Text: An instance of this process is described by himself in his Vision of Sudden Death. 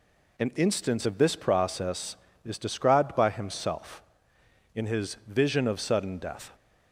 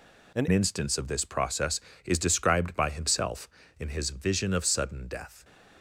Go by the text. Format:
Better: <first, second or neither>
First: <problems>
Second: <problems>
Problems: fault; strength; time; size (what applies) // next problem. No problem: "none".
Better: first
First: none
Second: changes voice at "instance"; from 0.5 s on; 4.9 s long // stays silent after the last word; slight; from 5.2 s on; 0.6 s long